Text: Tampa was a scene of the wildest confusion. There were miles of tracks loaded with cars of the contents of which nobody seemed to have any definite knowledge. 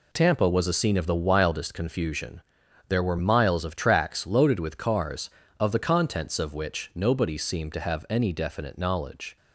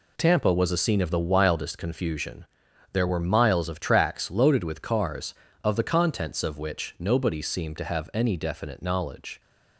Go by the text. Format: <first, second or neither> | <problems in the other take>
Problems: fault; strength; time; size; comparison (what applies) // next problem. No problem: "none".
neither | none